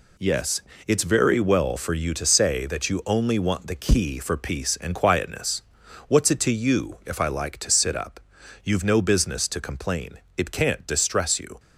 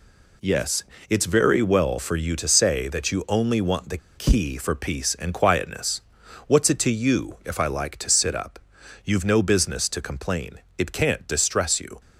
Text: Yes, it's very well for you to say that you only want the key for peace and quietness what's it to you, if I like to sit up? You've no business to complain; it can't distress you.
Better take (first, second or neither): first